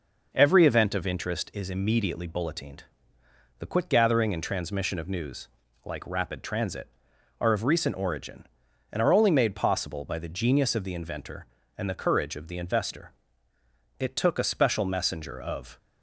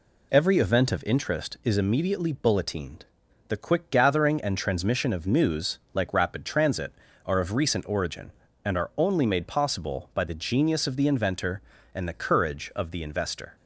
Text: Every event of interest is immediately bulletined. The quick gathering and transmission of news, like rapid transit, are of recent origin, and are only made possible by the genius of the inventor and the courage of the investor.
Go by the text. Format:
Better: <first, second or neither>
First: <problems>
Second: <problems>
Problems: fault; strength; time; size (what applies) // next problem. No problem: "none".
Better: second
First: goes on to say "It took a special messenger of"; strong; from 13.9 s on; 1.7 s long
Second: none